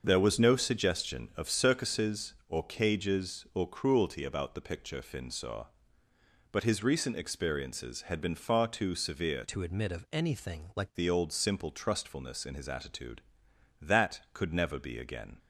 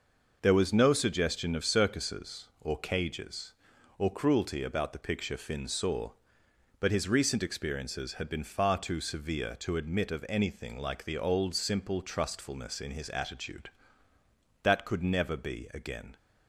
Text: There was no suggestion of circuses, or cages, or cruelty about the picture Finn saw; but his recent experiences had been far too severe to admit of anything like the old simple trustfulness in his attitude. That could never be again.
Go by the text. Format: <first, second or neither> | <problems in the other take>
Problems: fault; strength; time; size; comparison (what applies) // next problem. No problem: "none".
second | starts louder than the rest; until 1.0 s; 6.5 dB // changes voice from "to" to "like"; from 9.4 to 10.9 s; 1.5 s long